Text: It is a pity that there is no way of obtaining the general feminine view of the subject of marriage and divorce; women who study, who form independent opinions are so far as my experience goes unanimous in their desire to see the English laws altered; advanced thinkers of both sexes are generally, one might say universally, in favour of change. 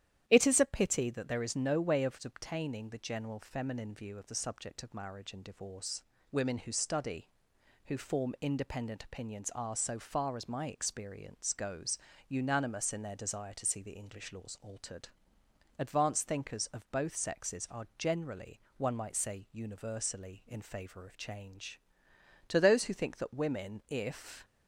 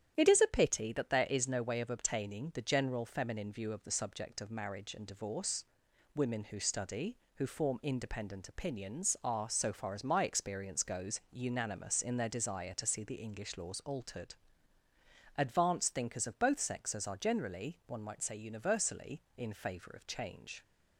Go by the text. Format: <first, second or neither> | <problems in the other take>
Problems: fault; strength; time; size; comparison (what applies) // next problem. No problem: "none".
second | starts louder than the rest; strong; until 1.3 s; 11 dB; strong in the second // pauses between "goes" and "unanimous"; slight; at 11.9 s; 0.32 s long // goes on to say "To those who think that women if"; strong; from 22.4 s on; 1.9 s long